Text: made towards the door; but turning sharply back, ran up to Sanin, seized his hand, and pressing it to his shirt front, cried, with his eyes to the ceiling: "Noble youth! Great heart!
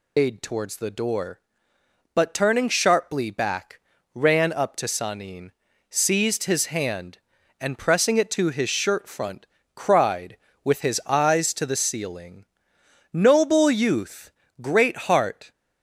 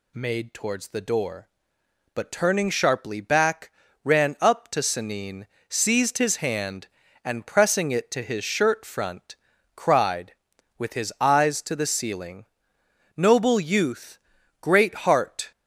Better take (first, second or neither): second